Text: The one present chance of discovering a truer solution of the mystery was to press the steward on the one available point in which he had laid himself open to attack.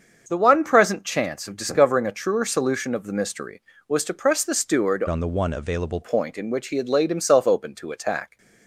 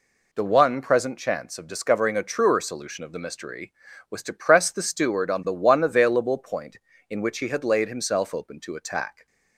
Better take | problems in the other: second | starts louder than the rest; until 1.2 s; 6.5 dB // changes voice from "on" to "available"; from 5.0 to 6.0 s; 1.0 s long

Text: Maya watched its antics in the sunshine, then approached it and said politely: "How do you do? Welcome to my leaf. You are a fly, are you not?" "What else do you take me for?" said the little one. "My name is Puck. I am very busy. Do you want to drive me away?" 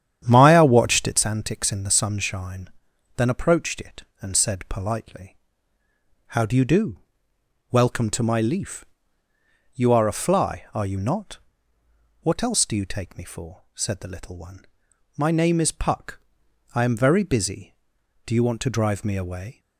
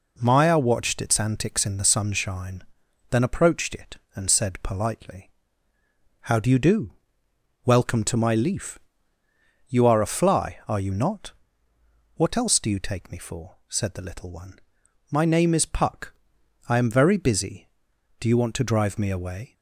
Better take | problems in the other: second | starts louder than the rest; strong; until 1.2 s; 9.5 dB

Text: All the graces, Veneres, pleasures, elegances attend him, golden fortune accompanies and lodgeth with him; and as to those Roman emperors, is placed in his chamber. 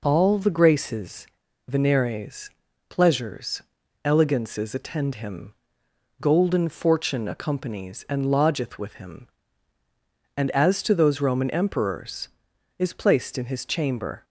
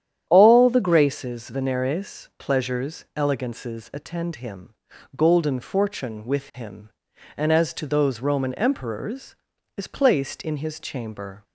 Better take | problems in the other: first | starts louder than the rest; strong; until 1.3 s; 10 dB // skips "accompanies and lodgeth"; at 6.2 s

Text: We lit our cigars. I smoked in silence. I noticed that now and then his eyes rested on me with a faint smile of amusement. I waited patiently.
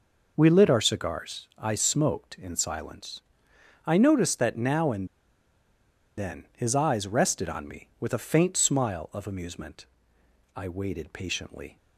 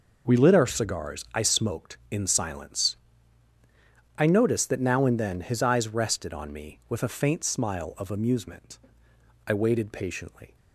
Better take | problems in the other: second | pauses between "and" and "then"; at 5.0 s; 1.1 s long

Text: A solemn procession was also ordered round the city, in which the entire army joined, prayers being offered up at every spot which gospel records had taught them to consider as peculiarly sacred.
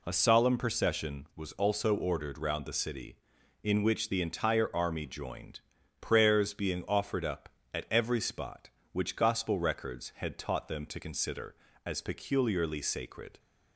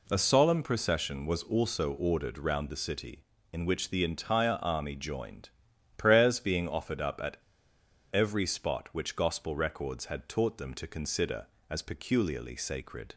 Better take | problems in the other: first | pauses between "at" and "every"; noticeable; at 7.3 s; 0.74 s long

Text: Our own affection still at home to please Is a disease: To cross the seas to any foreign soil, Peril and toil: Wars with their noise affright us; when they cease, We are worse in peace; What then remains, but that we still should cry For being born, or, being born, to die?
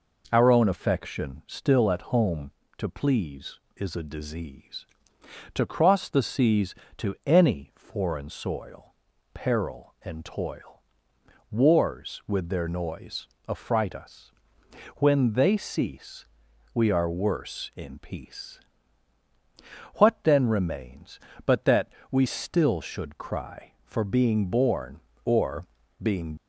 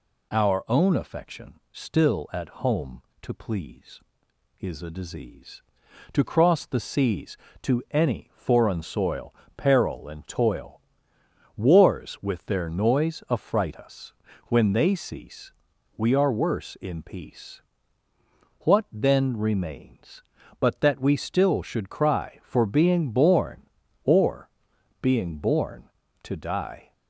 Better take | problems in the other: second | pauses between "noise" and "affright"; slight; at 13.2 s; 0.22 s long // pauses between "that" and "we"; slight; at 21.9 s; 0.18 s long // stops before "born to die"; at 26.3 s

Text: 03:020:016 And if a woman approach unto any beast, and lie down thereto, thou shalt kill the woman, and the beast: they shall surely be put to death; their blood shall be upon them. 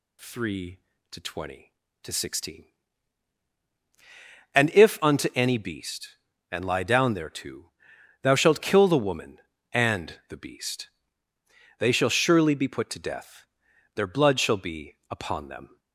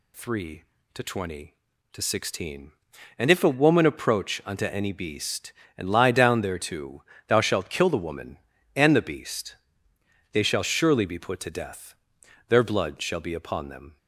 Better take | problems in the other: second | skips "a woman approach"; at 4.9 s

